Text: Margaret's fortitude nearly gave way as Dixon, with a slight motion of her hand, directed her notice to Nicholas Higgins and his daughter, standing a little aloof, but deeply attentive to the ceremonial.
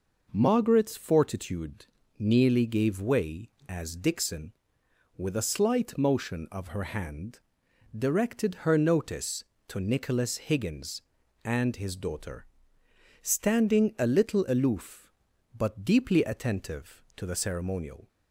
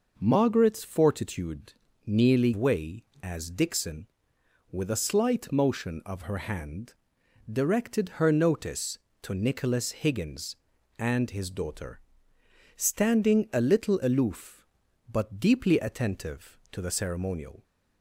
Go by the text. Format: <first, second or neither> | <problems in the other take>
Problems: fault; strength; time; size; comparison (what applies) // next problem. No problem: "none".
first | pauses between "fortitude" and "nearly"; slight; at 1.7 s; 0.32 s long; slight in the first // skips "gave"; at 2.5 s